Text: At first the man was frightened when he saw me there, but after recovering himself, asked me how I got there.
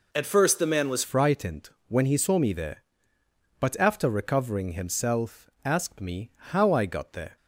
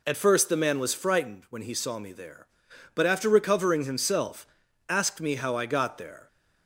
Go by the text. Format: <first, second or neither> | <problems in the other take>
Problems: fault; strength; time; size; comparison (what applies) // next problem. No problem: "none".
second | changes voice at "frightened"; from 1.0 s on; 6.3 s long // pauses between "frightened" and "when"; slight; at 1.6 s; 0.20 s long // pauses between "me" and "how"; slight; at 6.3 s; 0.22 s long